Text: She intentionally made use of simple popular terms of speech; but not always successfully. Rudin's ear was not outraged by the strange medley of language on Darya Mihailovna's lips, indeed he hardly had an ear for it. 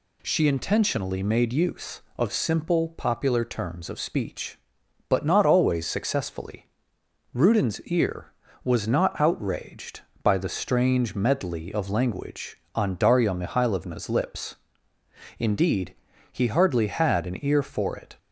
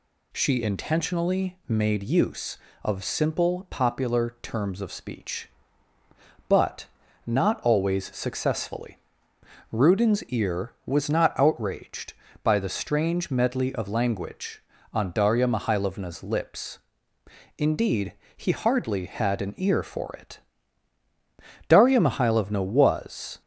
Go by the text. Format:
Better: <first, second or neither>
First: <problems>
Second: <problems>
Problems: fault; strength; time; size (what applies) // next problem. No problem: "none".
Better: first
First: pauses between "indeed" and "he"; slight; at 15.9 s; 0.34 s long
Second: pauses between "but" and "not"; at 6.8 s; 0.40 s long // pauses between "indeed" and "he"; slight; at 18.1 s; 0.24 s long // goes on to say "Darya Mihailovna was"; strong; from 21.6 s on; 1.7 s long